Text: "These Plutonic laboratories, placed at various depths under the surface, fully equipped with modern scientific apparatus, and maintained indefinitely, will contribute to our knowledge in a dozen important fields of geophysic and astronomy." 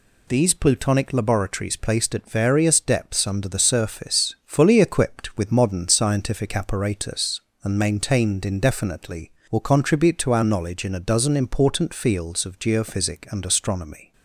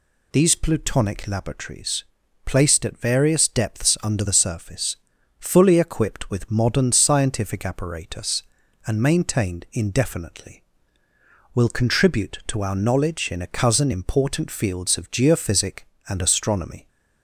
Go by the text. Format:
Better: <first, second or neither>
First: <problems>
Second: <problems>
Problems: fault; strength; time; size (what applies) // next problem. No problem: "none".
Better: first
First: none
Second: says "cousin" for "dozen"; at 13.4 s